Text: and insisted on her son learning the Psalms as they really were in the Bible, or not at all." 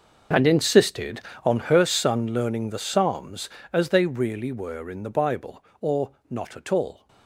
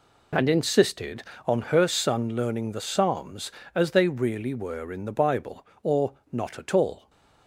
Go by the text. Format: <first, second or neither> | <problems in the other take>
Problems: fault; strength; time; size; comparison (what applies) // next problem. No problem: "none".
second | gets quieter; strong; throughout; 17 dB // pauses between "or" and "not"; slight; at 6.1 s; 0.18 s long; slight in the second